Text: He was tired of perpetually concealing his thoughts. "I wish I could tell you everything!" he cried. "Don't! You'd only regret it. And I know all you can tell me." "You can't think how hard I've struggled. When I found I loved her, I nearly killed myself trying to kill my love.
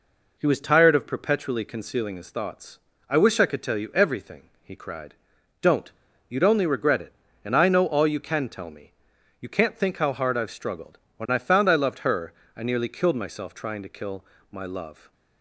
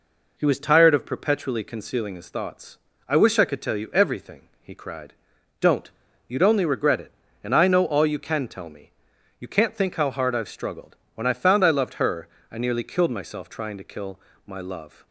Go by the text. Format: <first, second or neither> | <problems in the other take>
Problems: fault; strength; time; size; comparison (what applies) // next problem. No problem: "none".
neither | pauses between "kill" and "my"; slight; the same in both